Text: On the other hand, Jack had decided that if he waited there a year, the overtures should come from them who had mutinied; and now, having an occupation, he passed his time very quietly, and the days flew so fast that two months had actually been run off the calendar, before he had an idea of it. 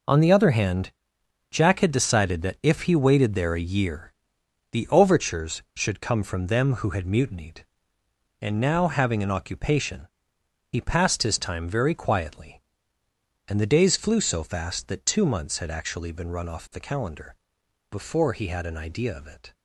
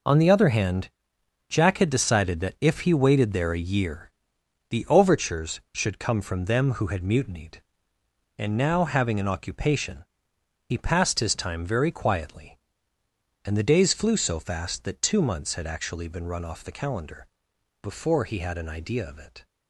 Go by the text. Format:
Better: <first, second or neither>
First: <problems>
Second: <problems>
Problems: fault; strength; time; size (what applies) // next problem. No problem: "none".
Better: neither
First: none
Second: none